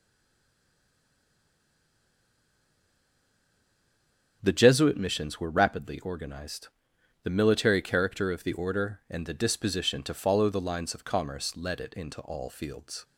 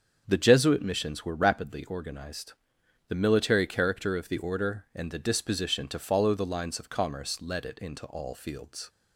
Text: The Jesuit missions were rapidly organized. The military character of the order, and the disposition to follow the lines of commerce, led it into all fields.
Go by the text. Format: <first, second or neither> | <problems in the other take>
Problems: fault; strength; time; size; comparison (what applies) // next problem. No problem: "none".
second | stays silent before the first word; strong; until 4.4 s; 4.4 s long // starts louder than the rest; until 5.4 s; 7 dB; also in the second